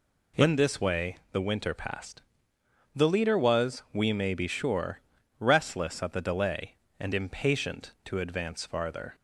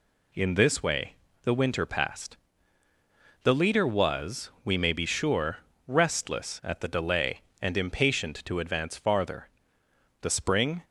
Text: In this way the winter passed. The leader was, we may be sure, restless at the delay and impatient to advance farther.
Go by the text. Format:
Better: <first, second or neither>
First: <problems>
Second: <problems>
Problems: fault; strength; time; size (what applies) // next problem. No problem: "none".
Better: first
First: none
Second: pauses between "way" and "the"; slight; at 1.1 s; 0.30 s long // goes on to say "The spring"; noticeable; from 10.2 s on; 0.62 s long